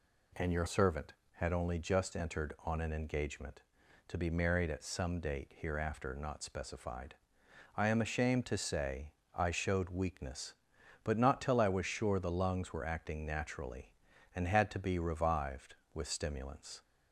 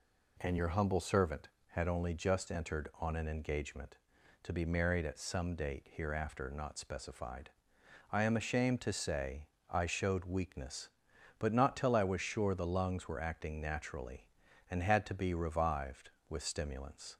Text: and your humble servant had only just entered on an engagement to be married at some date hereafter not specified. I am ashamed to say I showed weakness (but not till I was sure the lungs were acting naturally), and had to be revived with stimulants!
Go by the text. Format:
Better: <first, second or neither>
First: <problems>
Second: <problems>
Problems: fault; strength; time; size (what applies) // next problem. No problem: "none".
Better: second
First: skips "humble"; at 0.6 s // pauses between "say" and "I"; slight; at 9.1 s; 0.22 s long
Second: pauses between "say" and "I"; slight; at 9.4 s; 0.22 s long